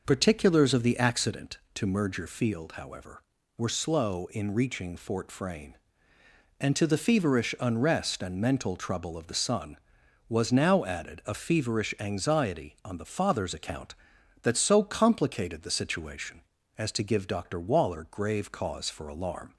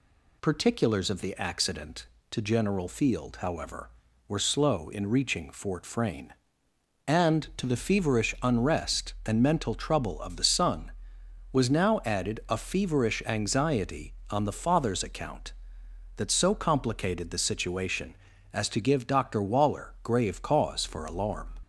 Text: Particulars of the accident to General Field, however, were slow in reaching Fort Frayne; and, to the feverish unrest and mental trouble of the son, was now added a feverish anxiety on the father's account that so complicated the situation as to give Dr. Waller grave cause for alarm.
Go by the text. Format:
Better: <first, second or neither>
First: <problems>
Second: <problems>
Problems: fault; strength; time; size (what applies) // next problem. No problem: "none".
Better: second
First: says "Merger" for "General"; at 1.8 s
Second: none